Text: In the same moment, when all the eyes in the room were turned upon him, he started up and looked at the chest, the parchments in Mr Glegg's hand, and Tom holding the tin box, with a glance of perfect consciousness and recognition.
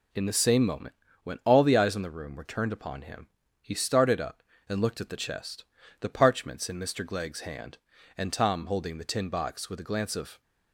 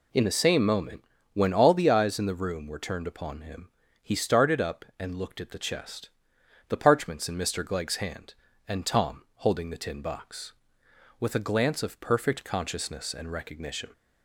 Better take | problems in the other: second | stops before "perfect consciousness and recognition"; at 10.4 s

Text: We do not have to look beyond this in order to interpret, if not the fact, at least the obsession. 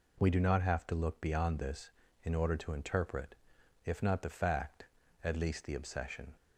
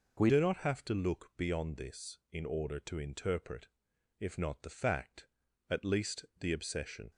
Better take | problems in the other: first | changes voice at "do"; from 0.2 s on; 6.9 s long

